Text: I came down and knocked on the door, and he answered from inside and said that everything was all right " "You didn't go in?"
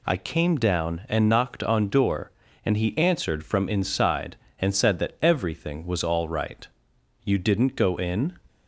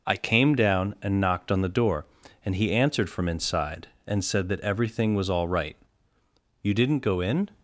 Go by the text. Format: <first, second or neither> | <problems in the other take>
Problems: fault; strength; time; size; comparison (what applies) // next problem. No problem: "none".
second | skips "the"; at 1.8 s